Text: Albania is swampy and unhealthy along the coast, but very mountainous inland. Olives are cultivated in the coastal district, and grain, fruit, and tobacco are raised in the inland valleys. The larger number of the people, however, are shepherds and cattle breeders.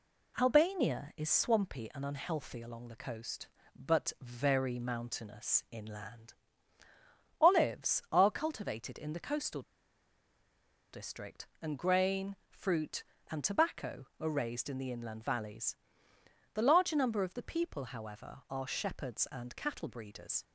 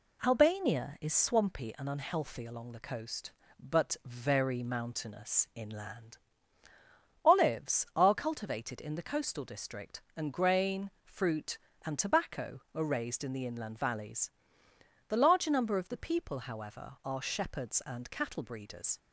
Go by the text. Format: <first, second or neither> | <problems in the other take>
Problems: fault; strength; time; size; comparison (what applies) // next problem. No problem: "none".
second | pauses between "coastal" and "district"; strong; at 9.6 s; 1.3 s long